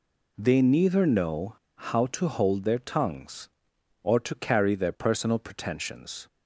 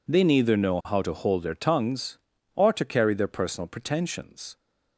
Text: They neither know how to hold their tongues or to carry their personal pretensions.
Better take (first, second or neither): second